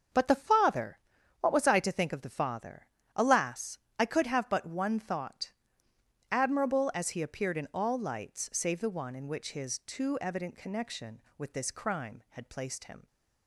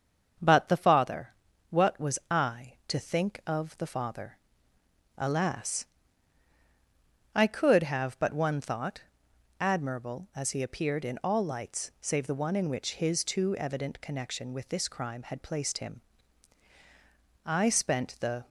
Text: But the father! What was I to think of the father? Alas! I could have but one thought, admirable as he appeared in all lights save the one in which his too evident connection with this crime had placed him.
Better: first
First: starts louder than the rest; until 1.5 s; 7 dB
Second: starts louder than the rest; until 1.8 s; 7 dB // goes on to say "I spent the"; noticeable; from 17.4 s on; 1.0 s long

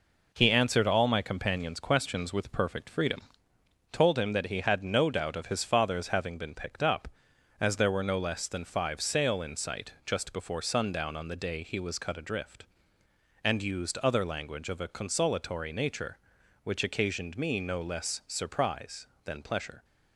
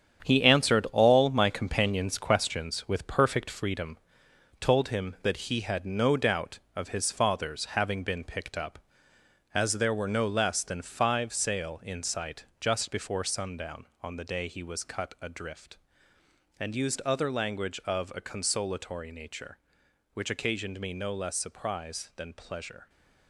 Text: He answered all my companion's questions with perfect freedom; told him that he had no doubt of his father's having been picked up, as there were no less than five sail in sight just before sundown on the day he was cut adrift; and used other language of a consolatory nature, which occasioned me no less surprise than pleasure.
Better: first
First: none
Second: gets quieter; strong; throughout; 9 dB

